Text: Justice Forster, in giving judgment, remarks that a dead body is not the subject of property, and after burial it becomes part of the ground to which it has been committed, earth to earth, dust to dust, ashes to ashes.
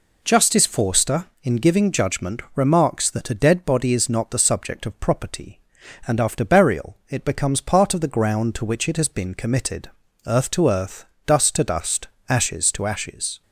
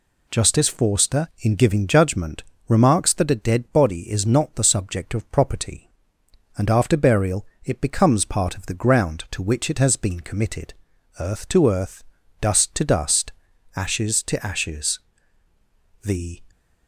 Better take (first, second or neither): first